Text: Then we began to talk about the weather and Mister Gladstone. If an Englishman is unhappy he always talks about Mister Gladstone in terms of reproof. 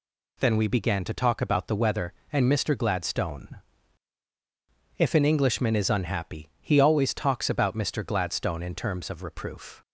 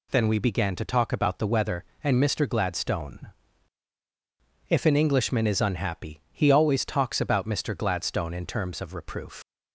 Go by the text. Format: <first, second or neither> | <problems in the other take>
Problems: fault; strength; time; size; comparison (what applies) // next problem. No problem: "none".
first | leaves "reproof" unfinished; at 9.4 s; 100 ms